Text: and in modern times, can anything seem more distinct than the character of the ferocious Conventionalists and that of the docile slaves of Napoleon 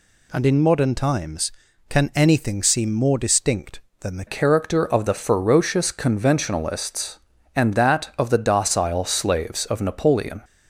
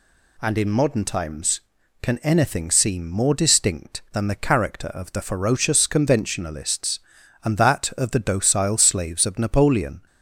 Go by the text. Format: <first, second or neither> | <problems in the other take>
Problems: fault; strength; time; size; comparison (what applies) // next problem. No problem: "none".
second | changes voice at "character"; from 4.2 s on; 6.2 s long